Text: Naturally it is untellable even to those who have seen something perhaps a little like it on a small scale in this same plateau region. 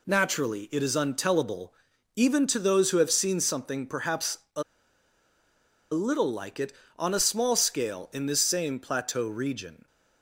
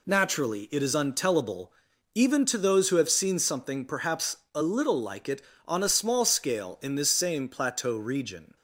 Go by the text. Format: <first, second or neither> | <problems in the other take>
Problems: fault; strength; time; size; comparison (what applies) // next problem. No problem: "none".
second | pauses between "untellable" and "even"; at 1.7 s; 0.42 s long; also in the second // pauses between "perhaps" and "a"; slight; at 4.3 s; 0.18 s long; slight in the second // pauses between "a" and "little"; strong; at 4.6 s; 1.3 s long